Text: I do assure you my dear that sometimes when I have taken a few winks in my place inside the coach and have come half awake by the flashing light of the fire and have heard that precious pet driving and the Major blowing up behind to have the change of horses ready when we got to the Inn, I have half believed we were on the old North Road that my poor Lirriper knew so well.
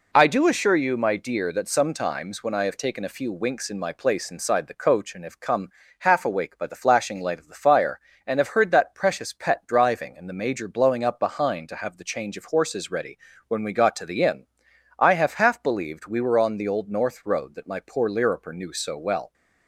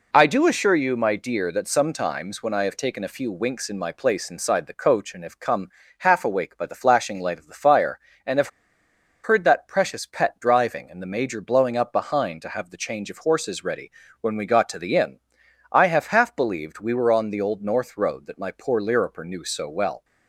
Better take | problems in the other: first | pauses between "come" and "half"; slight; at 5.6 s; 0.30 s long; slight in the first // pauses between "have" and "heard"; noticeable; at 8.4 s; 0.74 s long // pauses between "ready" and "when"; slight; at 13.9 s; 0.30 s long; slight in the first

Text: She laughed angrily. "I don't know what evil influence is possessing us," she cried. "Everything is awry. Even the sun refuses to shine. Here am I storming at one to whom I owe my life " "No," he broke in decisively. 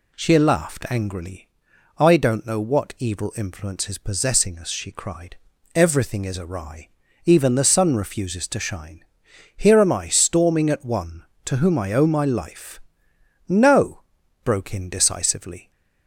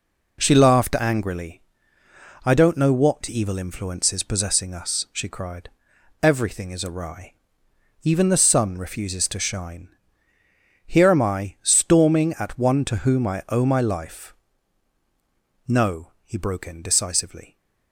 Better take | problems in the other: second | skips "he"; at 14.2 s

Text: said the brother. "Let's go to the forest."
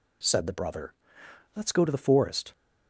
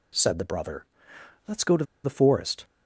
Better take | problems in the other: first | pauses between "to" and "the"; slight; at 1.8 s; 0.20 s long

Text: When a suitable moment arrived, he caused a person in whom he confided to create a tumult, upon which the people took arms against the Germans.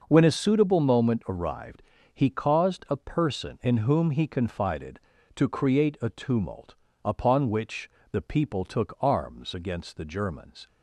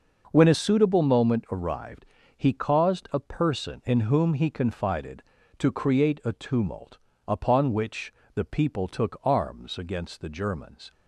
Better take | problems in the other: neither | pauses between "which" and "the"; slight; the same in both

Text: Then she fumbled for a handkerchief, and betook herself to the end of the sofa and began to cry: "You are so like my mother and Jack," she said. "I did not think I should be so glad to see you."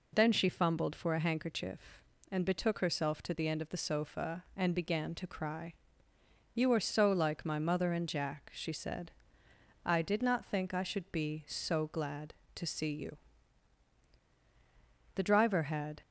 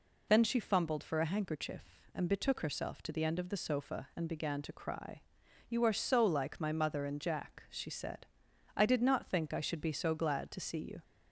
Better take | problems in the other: second | goes on to say "The driver had"; noticeable; from 15.1 s on; 0.86 s long

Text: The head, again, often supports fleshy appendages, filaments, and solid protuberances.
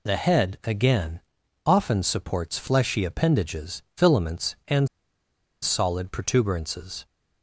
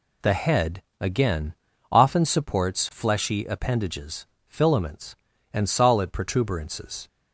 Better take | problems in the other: second | pauses between "and" and "solid"; noticeable; at 4.8 s; 0.75 s long

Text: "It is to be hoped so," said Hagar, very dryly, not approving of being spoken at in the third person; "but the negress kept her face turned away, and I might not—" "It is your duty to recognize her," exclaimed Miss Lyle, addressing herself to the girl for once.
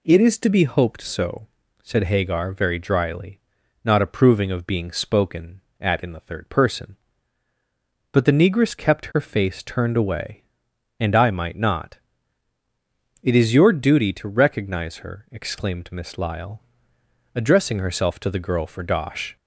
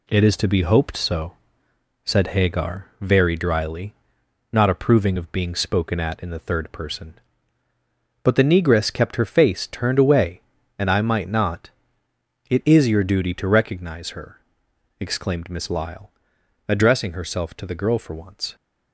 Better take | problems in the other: second | says "dosh" for "once"; at 18.8 s

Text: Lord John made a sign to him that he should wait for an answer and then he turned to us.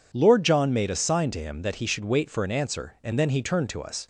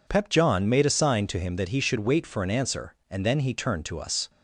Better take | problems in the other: first | says "Pep" for "Lord"; at 0.0 s

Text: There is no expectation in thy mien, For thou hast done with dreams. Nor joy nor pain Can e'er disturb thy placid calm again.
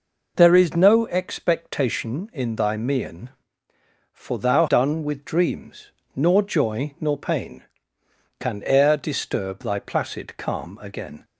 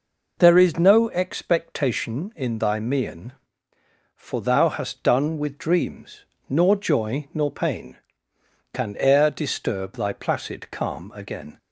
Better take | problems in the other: second | skips "hast"; at 4.6 s

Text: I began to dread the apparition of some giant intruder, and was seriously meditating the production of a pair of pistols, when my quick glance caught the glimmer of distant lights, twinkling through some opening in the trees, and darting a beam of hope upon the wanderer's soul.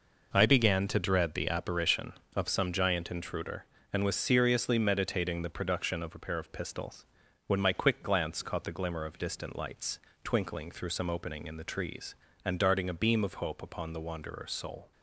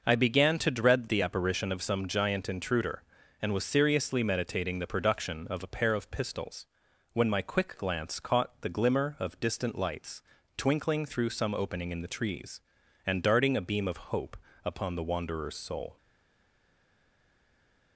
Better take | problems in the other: first | pauses between "hope" and "upon"; slight; at 14.3 s; 0.28 s long // stays silent after the last word; noticeable; from 15.9 s on; 2.0 s long

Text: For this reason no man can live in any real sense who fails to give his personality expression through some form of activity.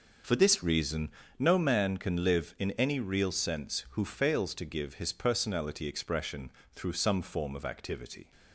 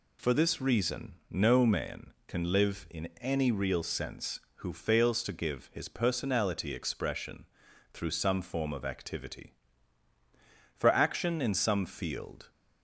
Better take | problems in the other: first | pauses between "reason" and "no"; slight; at 1.1 s; 0.16 s long; slight in the first // pauses between "expression" and "through"; noticeable; at 7.4 s; 0.48 s long; slight in the first // goes on to say "For action in some field"; strong; from 10.7 s on; 1.7 s long

